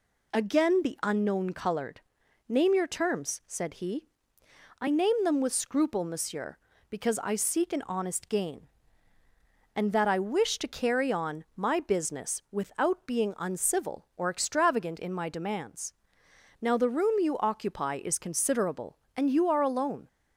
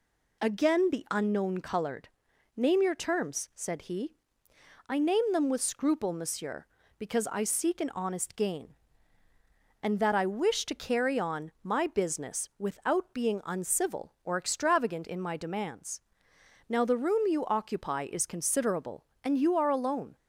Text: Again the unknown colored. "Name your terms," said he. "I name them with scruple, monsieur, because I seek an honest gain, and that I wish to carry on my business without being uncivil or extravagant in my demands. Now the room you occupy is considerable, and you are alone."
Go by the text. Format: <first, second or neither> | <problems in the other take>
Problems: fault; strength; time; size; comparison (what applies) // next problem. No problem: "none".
neither | none